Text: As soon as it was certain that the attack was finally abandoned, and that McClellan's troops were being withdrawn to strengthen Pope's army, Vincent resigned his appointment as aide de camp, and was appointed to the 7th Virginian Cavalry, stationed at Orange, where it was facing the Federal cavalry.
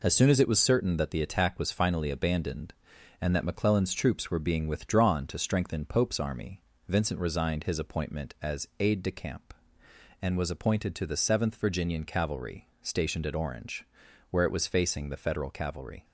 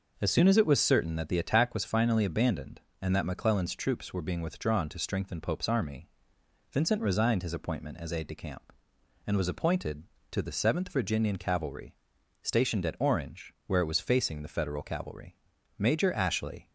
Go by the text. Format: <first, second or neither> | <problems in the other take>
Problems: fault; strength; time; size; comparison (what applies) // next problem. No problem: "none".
first | goes on to say "Major Ashley"; noticeable; from 15.7 s on; 0.92 s long